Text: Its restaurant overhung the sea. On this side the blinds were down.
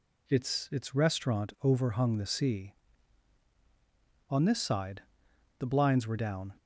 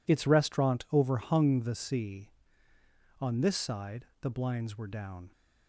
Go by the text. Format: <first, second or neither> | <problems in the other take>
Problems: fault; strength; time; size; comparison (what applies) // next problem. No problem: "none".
second | says "Its" twice; at 0.7 s // pauses between "side" and "the"; noticeable; at 5.0 s; 0.58 s long; slight in the second